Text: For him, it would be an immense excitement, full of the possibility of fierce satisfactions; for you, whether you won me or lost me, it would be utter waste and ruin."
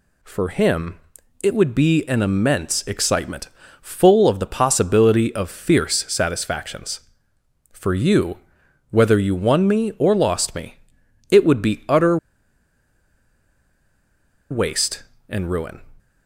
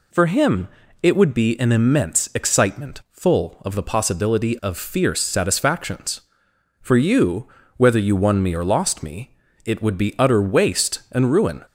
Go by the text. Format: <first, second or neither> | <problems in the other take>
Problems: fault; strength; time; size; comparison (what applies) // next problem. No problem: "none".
second | pauses between "utter" and "waste"; strong; at 12.1 s; 2.3 s long